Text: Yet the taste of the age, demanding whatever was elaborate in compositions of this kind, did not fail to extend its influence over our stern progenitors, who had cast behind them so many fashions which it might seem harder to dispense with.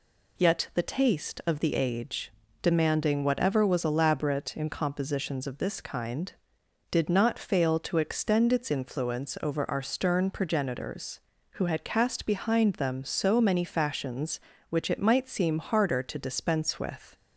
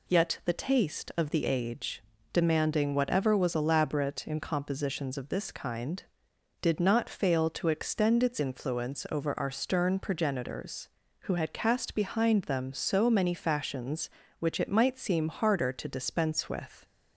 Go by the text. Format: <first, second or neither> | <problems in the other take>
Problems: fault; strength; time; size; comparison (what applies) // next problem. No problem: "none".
neither | none